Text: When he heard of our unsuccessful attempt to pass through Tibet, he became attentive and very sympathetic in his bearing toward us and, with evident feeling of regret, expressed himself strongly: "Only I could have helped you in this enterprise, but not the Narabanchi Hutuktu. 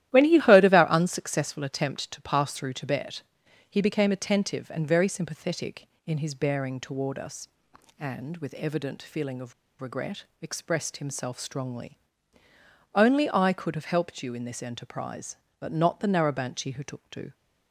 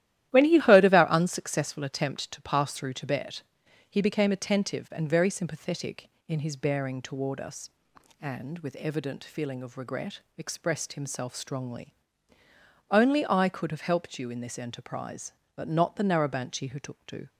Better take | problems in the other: second | starts louder than the rest; strong; until 1.1 s; 13 dB; strong in the second // pauses between "of" and "regret"; slight; at 9.5 s; 0.27 s long

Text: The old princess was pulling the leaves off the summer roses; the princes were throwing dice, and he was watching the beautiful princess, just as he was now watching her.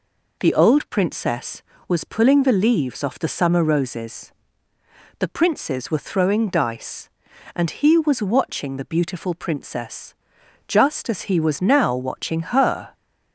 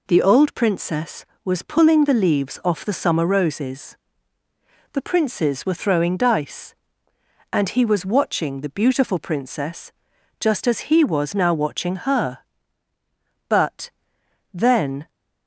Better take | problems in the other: first | goes on to say "But then"; from 13.4 s on; 1.6 s long

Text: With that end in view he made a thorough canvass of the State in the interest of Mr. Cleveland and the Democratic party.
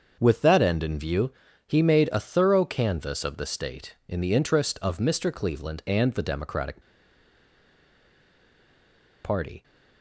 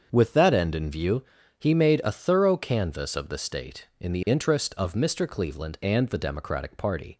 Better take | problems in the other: second | starts louder than the rest; until 1.2 s; 6.5 dB; also in the second // pauses between "view" and "he"; slight; at 1.2 s; 0.34 s long; slight in the second // pauses between "Democratic" and "party"; strong; at 6.8 s; 2.4 s long

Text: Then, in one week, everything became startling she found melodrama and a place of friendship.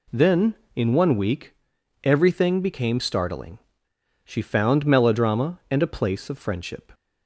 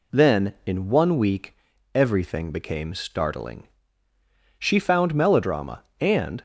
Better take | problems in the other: first | pauses between "startling" and "she"; noticeable; at 3.6 s; 0.96 s long; noticeable in the first // stops before "a place of friendship"; at 6.3 s

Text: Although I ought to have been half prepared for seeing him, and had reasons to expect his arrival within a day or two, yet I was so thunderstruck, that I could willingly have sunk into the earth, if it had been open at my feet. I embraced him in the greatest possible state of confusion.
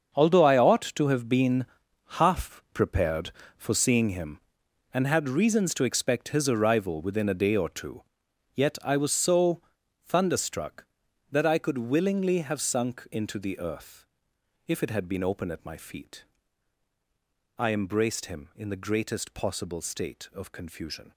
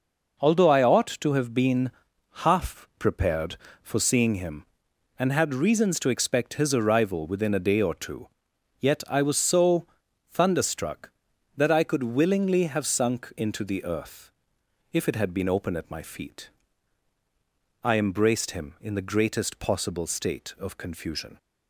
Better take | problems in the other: second | gets quieter; strong; throughout; 12.5 dB // pauses between "been" and "half"; noticeable; at 1.6 s; 0.52 s long; noticeable in the second // pauses between "so" and "thunderstruck"; at 9.6 s; 0.44 s long; also in the second

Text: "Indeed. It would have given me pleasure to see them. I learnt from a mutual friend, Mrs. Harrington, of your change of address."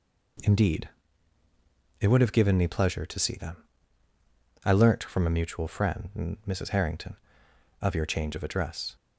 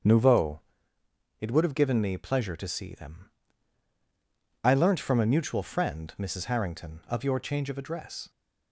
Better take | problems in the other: first | starts louder than the rest; strong; until 1.8 s; 7.5 dB // says "Nouveau" for "Indeed"; at 0.0 s

